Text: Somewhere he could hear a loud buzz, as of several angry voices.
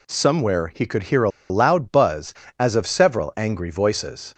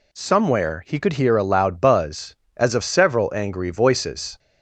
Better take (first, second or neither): second